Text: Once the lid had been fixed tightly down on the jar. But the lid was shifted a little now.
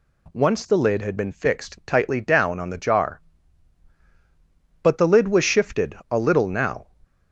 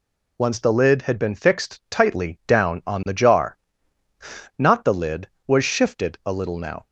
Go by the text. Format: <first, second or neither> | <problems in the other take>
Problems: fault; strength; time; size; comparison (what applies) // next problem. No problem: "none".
first | says "Not" for "But"; at 4.5 s